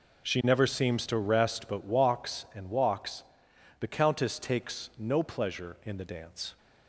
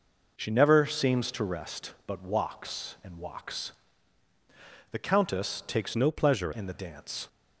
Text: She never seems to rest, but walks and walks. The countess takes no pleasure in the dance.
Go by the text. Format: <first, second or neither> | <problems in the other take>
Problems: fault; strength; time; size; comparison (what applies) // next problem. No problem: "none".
first | changes voice from "no" to "pleasure"; from 5.9 to 6.5 s; 0.6 s long